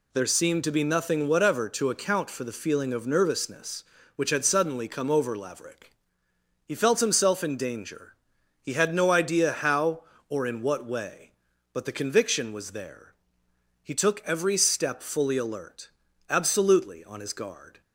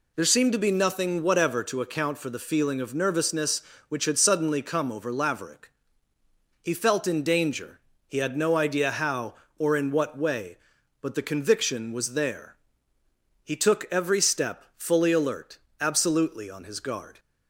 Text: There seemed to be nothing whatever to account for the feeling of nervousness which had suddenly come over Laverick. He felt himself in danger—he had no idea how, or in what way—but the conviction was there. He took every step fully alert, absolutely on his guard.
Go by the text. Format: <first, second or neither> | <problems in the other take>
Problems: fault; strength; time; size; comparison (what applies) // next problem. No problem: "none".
first | skips "himself"; at 7.0 s